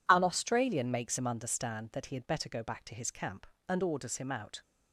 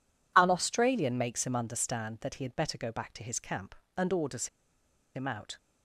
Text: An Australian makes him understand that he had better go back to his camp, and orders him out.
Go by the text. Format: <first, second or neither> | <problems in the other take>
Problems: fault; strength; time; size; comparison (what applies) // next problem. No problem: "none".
first | pauses between "orders" and "him"; noticeable; at 4.4 s; 0.67 s long